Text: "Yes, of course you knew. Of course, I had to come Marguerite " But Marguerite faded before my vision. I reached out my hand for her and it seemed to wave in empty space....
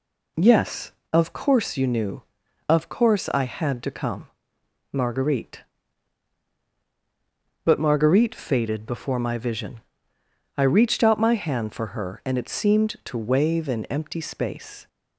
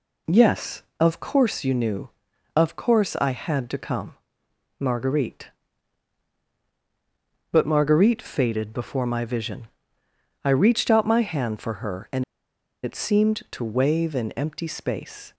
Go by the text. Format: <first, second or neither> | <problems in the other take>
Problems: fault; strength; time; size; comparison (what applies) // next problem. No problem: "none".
first | pauses between "come" and "Marguerite"; noticeable; at 4.1 s; 0.62 s long; noticeable in the first // pauses between "and" and "it"; noticeable; at 12.2 s; 0.60 s long